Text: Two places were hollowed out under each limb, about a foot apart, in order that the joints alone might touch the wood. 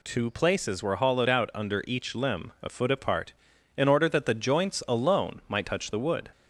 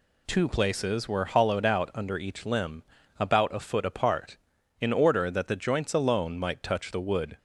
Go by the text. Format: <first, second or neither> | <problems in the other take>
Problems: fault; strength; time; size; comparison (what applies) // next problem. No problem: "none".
second | skips "about"; at 2.5 s